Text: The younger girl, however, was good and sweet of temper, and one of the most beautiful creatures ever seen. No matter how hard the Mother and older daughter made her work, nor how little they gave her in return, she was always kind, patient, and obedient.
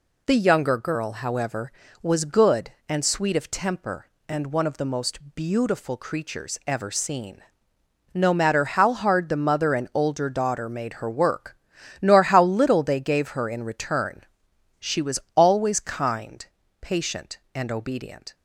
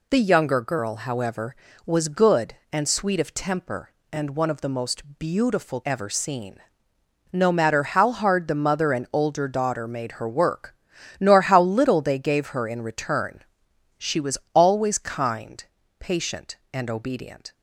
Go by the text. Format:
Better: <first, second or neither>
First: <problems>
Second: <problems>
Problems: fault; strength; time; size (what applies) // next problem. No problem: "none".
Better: first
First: pauses between "most" and "beautiful"; slight; at 5.1 s; 0.16 s long // pauses between "was" and "always"; slight; at 15.1 s; 0.16 s long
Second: pauses between "most" and "beautiful"; slight; at 5.0 s; 0.16 s long // skips "creatures"; at 5.8 s // pauses between "was" and "always"; slight; at 14.3 s; 0.16 s long